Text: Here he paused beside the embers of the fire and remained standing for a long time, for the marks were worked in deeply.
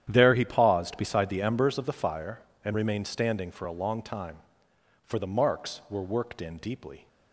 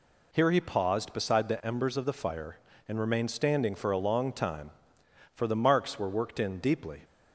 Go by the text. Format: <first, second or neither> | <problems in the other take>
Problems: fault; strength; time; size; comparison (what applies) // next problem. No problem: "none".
second | starts louder than the rest; strong; until 1.1 s; 10.5 dB // says "There" for "Here"; at 0.1 s